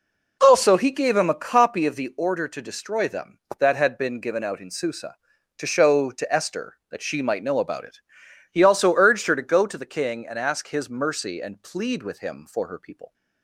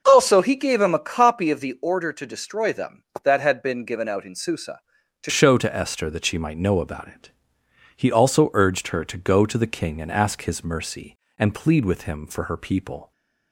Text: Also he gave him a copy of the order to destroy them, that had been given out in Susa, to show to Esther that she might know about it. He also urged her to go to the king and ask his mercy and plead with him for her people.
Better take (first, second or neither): first